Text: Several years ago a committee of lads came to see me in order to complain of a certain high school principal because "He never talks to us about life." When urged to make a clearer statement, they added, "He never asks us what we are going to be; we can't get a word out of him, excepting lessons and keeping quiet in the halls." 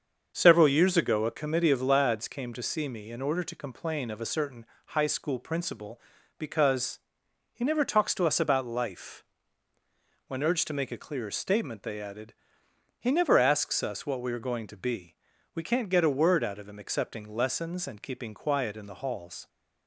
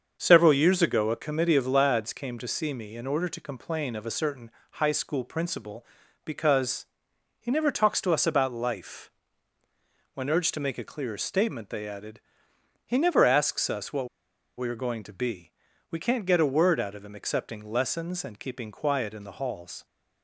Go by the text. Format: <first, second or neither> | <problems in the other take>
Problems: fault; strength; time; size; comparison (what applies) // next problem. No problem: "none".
first | starts louder than the rest; until 1.2 s; 6.5 dB; also in the first // pauses between "certain" and "high"; slight; at 4.4 s; 0.22 s long; slight in the first // pauses between "because" and "He"; noticeable; at 6.8 s; 0.54 s long; noticeable in the first // pauses between "what" and "we"; noticeable; at 14.0 s; 0.50 s long